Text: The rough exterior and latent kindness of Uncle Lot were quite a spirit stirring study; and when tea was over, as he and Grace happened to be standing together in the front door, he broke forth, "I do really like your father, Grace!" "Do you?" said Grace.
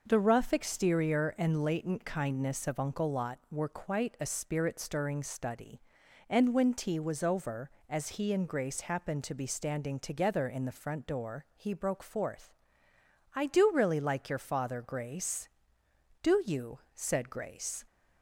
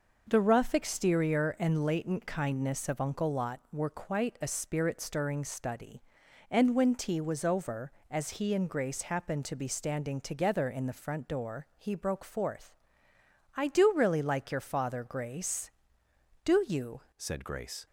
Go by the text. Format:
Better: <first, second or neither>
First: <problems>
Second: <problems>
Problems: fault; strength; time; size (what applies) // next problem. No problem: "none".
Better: first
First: none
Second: changes voice at "said"; from 17.1 s on; 0.7 s long